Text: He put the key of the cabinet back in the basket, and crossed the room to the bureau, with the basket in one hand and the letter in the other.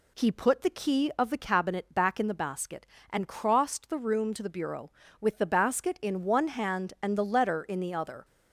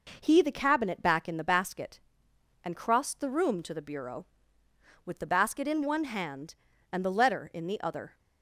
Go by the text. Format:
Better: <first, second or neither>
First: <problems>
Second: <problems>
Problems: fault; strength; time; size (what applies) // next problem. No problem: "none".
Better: first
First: none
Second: skips "put the key of"; at 0.4 s